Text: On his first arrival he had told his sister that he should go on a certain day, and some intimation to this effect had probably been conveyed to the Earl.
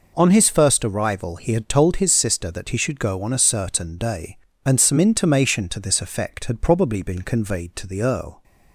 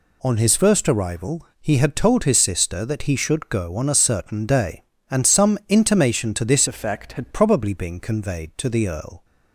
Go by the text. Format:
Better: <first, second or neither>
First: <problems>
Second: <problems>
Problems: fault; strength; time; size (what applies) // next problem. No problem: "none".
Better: first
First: none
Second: changes voice from "effect" to "had"; from 6.6 to 7.3 s; 0.7 s long